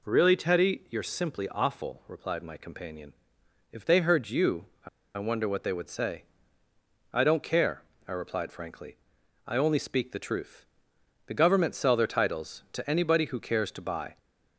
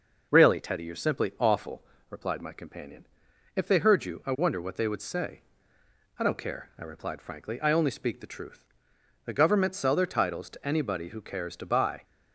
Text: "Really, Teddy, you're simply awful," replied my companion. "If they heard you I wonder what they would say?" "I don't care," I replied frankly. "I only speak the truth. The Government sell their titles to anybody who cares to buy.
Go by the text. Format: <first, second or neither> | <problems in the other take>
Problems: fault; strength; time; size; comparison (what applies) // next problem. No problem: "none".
second | pauses between "you" and "I"; slight; at 4.6 s; 0.18 s long // pauses between "I" and "wonder"; slight; at 4.8 s; 0.28 s long